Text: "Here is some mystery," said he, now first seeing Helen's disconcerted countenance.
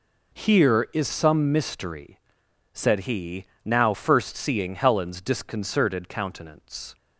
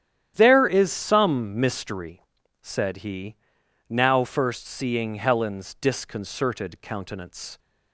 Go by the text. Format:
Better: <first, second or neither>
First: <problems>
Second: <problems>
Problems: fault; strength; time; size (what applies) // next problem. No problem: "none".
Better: first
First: none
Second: starts louder than the rest; strong; until 1.3 s; 10.5 dB // says "There" for "Here"; at 0.3 s